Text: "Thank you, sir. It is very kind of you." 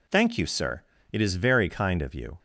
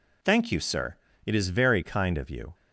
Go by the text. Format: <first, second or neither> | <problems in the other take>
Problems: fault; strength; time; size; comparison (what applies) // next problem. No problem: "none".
neither | none